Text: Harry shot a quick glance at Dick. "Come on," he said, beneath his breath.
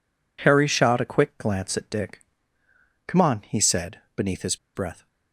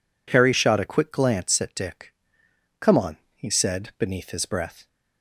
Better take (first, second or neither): second